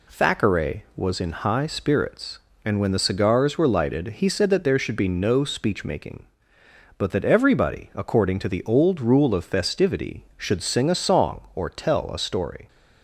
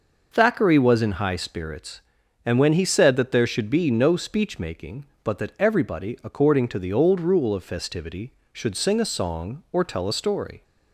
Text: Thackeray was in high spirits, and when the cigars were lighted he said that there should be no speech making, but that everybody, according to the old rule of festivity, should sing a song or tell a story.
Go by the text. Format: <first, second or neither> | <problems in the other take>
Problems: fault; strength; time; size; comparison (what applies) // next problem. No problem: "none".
first | skips "the cigars were lighted"; at 2.7 s